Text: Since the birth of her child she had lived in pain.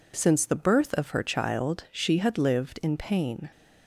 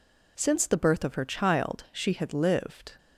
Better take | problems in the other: first | stops before "in pain"; at 2.9 s

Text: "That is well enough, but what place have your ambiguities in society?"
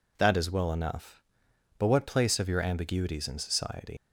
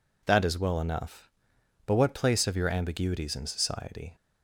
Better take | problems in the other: second | leaves "society" unfinished; at 3.9 s; 100 ms

